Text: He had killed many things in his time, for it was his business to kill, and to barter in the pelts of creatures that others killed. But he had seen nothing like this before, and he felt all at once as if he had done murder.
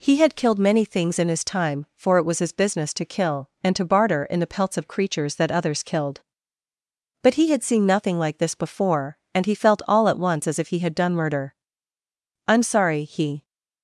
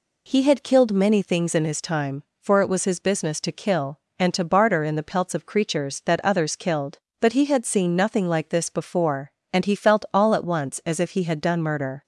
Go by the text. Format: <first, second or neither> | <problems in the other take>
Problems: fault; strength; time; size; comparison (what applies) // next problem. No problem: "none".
second | goes on to say "I'm sorry he"; noticeable; from 12.4 s on; 0.96 s long